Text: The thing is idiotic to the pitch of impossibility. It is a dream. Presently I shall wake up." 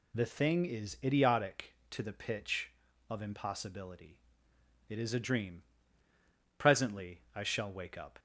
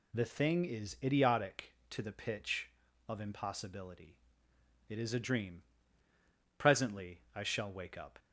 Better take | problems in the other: neither | none

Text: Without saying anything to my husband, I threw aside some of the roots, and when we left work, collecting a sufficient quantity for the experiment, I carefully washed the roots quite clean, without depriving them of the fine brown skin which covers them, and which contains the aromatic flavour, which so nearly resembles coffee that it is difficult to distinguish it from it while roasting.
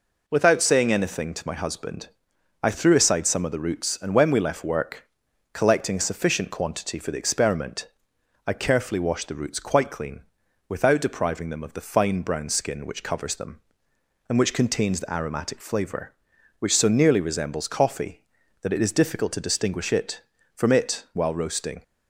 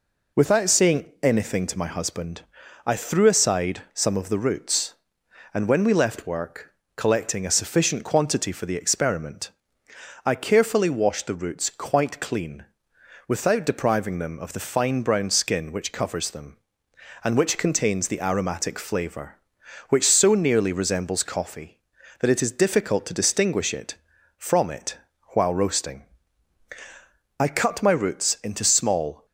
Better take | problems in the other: first | pauses between "it" and "while"; slight; at 24.9 s; 0.36 s long // goes on to say "I cut my roots into small"; strong; from 27.3 s on; 1.8 s long

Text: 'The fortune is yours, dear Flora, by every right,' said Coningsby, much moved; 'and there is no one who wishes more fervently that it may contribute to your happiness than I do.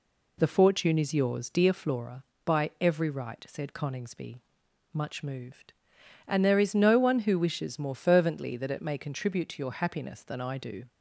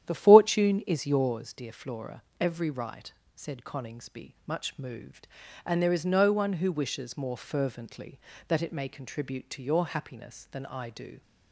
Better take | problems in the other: first | starts louder than the rest; strong; until 1.0 s; 10.5 dB // skips "by"; at 2.2 s

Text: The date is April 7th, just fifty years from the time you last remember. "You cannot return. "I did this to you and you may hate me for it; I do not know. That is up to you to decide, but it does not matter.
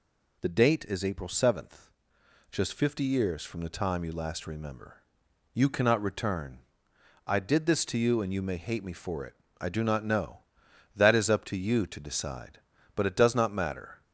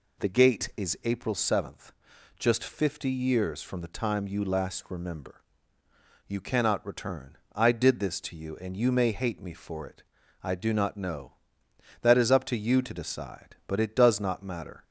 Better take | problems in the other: first | says "gate" for "date"; at 0.2 s

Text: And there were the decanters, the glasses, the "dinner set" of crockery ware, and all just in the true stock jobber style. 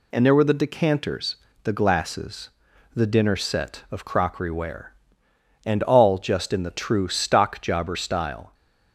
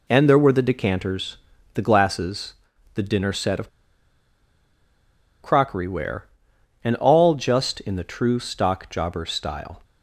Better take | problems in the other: first | pauses between "of" and "crockery"; strong; at 3.6 s; 1.7 s long

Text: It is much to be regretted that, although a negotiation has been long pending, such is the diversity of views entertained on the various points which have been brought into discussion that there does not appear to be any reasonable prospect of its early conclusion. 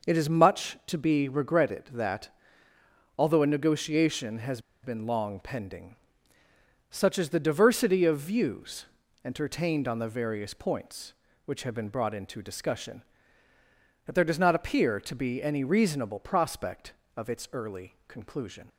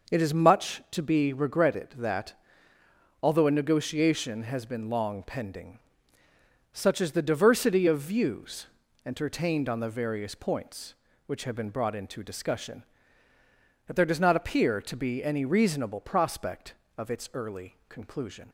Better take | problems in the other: second | pauses between "has" and "been"; slight; at 4.5 s; 0.23 s long // pauses between "views" and "entertained"; at 8.8 s; 0.40 s long; also in the second

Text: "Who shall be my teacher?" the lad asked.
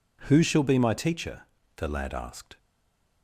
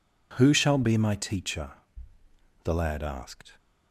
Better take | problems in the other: second | stays silent after the last word; slight; from 2.5 s on; 0.7 s long

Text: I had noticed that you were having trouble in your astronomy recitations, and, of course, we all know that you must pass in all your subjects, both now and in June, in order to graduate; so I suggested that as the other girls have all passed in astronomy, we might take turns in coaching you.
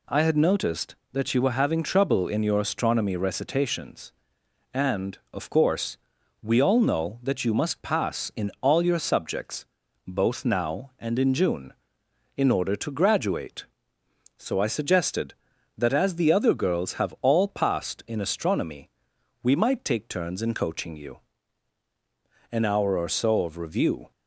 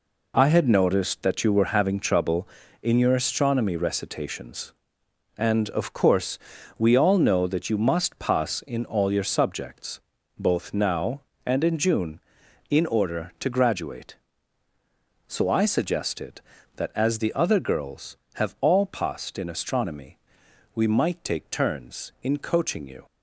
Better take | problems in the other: second | goes on to say "An hour or so of review"; from 22.5 s on; 1.6 s long

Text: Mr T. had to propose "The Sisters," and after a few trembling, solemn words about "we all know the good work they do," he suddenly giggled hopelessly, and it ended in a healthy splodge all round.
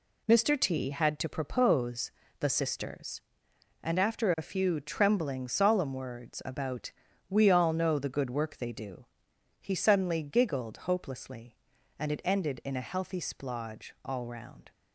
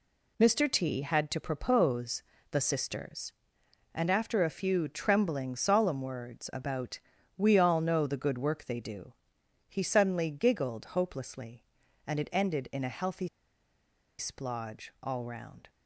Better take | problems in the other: first | pauses between "propose" and "The"; slight; at 2.2 s; 0.30 s long; slight in the first // pauses between "about" and "we"; at 6.9 s; 0.38 s long; also in the first // pauses between "healthy" and "splodge"; noticeable; at 13.2 s; 0.90 s long

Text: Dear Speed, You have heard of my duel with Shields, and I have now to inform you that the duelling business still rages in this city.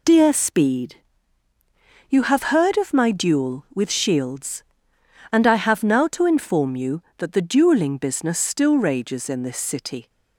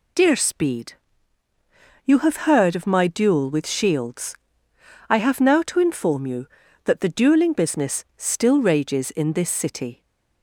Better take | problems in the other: first | skips "and"; at 4.7 s

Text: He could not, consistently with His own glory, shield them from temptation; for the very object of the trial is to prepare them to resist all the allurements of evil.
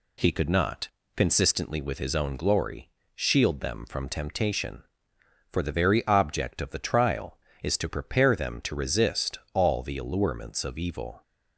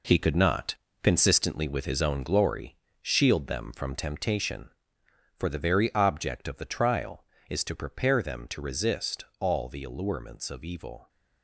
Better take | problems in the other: first | gets quieter; strong; throughout; 9 dB // pauses between "resist" and "all"; slight; at 9.2 s; 0.16 s long; slight in the first

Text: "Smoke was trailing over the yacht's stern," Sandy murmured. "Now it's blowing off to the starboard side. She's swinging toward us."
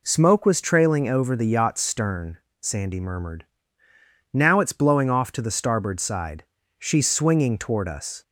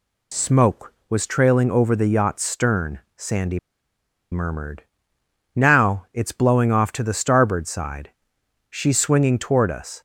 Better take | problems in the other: first | pauses between "Sandy" and "murmured"; noticeable; at 3.5 s; 0.73 s long

